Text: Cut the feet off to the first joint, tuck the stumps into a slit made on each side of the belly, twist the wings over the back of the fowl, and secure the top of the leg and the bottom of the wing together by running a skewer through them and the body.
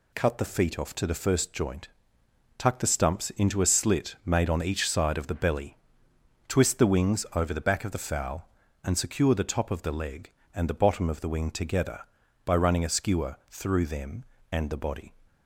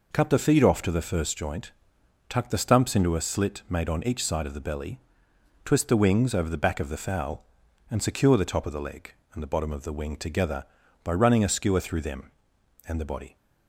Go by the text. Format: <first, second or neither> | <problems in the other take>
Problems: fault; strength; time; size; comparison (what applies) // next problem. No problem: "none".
neither | none